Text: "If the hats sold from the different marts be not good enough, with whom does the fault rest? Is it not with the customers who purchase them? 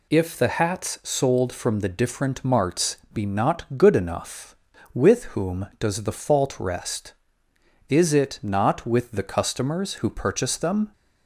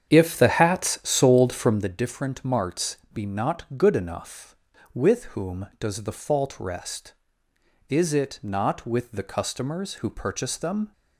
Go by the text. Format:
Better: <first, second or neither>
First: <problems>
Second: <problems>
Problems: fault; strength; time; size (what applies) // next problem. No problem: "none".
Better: first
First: pauses between "marts" and "be"; slight; at 2.9 s; 0.16 s long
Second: starts louder than the rest; strong; until 1.9 s; 8 dB // pauses between "marts" and "be"; slight; at 2.9 s; 0.16 s long